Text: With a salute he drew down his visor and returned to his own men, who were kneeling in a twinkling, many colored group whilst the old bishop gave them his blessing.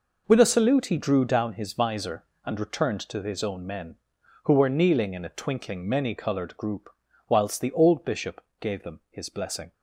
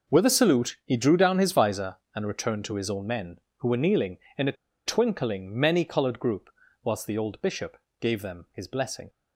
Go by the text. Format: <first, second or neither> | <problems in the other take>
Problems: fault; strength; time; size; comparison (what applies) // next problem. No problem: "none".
first | pauses between "a" and "twinkling"; slight; at 4.5 s; 0.32 s long // pauses between "group" and "whilst"; slight; at 6.5 s; 0.32 s long; also in the first // pauses between "bishop" and "gave"; slight; at 7.7 s; 0.24 s long; slight in the first